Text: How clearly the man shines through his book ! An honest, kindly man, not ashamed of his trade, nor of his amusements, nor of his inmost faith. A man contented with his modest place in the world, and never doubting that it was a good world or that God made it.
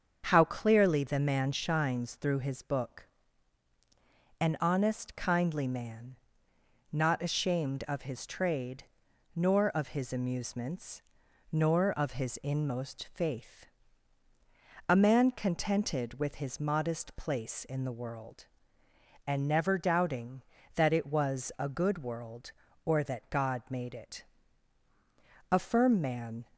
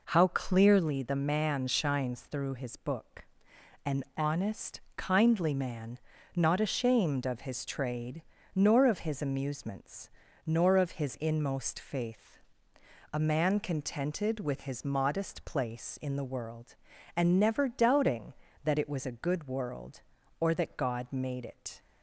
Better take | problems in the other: second | starts louder than the rest; until 1.2 s; 7 dB // goes on to say "A firm man"; noticeable; from 25.5 s on; 0.94 s long

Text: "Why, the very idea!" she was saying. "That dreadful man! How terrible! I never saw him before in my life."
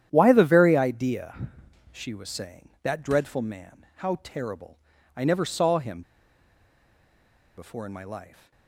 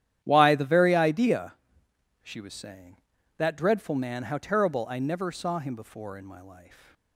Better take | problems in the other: second | starts louder than the rest; strong; until 1.1 s; 10 dB; strong in the second // pauses between "him" and "before"; strong; at 6.0 s; 1.5 s long

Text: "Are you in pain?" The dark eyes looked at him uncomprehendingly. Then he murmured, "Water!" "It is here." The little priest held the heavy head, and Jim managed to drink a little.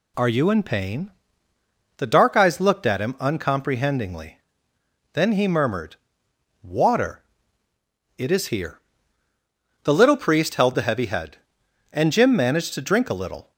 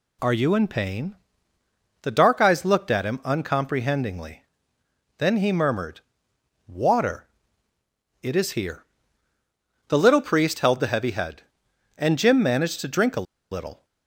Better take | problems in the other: first | pauses between "a" and "little"; slight; at 13.2 s; 0.28 s long

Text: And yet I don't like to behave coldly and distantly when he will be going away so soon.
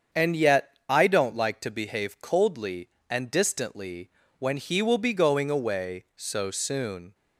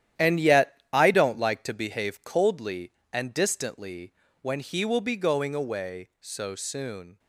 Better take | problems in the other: first | gets quieter; strong; throughout; 9 dB // starts louder than the rest; strong; until 1.3 s; 11 dB; strong in the first // pauses between "distantly" and "when"; slight; at 4.1 s; 0.28 s long; slight in the first

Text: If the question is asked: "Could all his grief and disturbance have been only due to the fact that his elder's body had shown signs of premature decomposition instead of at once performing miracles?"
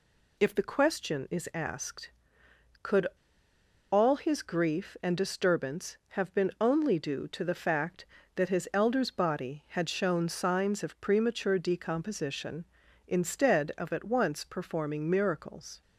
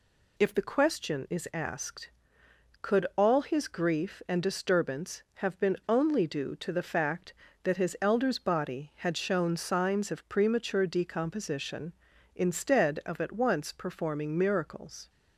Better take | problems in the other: second | pauses between "Could" and "all"; noticeable; at 3.0 s; 0.84 s long

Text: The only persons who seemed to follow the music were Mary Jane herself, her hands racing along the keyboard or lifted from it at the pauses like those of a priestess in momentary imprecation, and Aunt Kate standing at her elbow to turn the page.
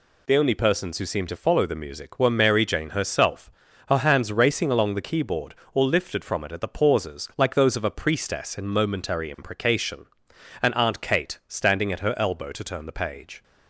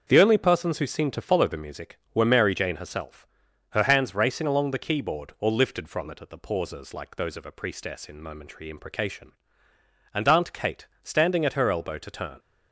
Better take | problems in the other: first | starts louder than the rest; until 1.0 s; 6.5 dB // pauses between "Kate" and "standing"; slight; at 10.8 s; 0.16 s long // stops before "the page"; at 12.3 s

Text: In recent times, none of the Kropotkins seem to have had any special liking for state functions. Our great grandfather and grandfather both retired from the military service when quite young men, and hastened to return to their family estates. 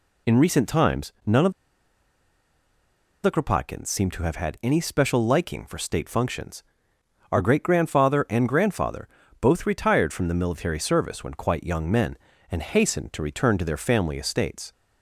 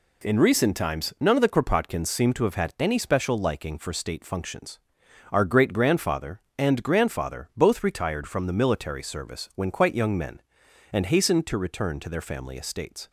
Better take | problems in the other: second | pauses between "of" and "the"; strong; at 1.5 s; 1.7 s long // pauses between "grandfather" and "both"; slight; at 9.0 s; 0.32 s long

